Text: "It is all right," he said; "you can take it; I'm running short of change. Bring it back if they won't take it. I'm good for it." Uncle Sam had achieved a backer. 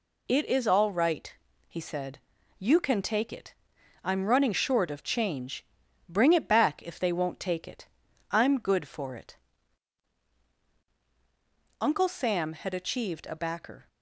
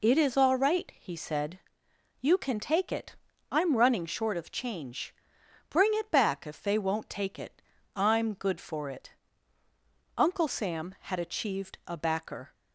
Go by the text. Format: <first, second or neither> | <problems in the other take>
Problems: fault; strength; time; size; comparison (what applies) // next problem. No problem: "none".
neither | none